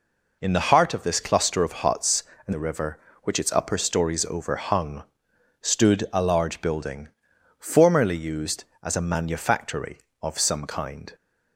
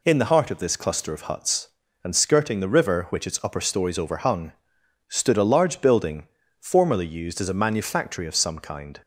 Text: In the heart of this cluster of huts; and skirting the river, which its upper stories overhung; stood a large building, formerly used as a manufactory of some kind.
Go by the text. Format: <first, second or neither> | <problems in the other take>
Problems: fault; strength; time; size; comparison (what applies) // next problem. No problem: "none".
second | skips "skirting"; at 2.5 s